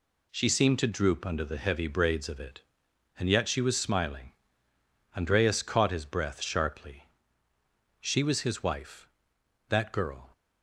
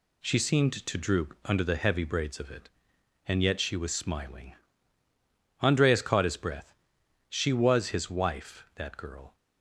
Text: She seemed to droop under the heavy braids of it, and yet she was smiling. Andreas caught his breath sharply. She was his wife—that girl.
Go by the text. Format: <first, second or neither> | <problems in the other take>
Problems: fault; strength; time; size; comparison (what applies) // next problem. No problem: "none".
first | skips "sharply"; at 7.0 s